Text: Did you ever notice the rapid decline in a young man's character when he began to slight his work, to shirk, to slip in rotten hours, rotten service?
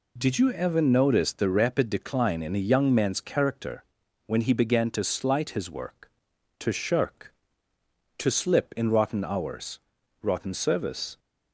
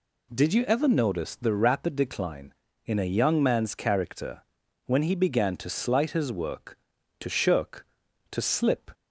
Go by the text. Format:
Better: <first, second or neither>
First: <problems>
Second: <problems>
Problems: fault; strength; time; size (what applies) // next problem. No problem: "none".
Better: first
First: pauses between "character" and "when"; at 3.8 s; 0.40 s long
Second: pauses between "character" and "when"; at 4.4 s; 0.42 s long // stops before "in rotten hours rotten service"; at 8.9 s